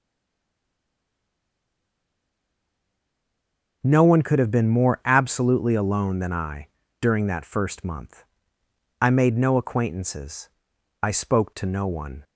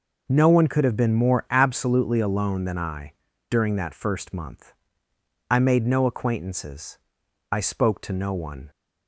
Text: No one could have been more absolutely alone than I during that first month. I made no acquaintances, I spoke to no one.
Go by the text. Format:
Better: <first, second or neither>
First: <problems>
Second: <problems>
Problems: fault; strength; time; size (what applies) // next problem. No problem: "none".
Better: second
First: stays silent before the first word; strong; until 3.8 s; 3.8 s long // pauses between "I" and "during"; slight; at 6.6 s; 0.34 s long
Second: pauses between "I" and "during"; at 3.1 s; 0.37 s long